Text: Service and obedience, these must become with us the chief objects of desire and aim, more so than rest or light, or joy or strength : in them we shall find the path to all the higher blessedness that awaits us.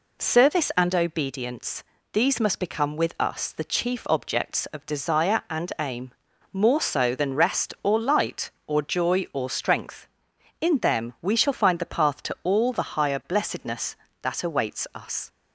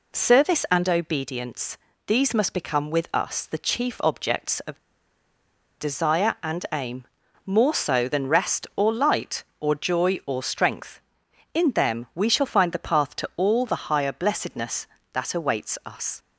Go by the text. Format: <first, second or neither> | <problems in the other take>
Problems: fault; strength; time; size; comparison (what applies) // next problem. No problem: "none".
first | pauses between "of" and "desire"; at 4.7 s; 1.0 s long